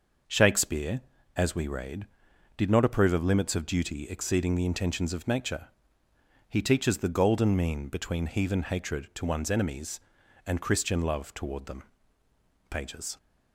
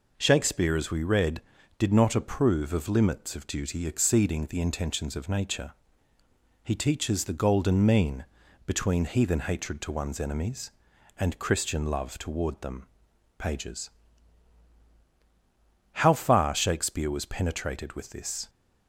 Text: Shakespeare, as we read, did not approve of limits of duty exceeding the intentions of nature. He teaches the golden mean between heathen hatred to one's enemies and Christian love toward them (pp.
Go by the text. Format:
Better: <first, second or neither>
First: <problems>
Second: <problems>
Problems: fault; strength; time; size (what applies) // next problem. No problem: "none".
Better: first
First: none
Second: pauses between "mean" and "between"; at 8.2 s; 0.40 s long // goes on to say "How far Shakespeare was penetrated with this"; strong; from 15.9 s on; 2.5 s long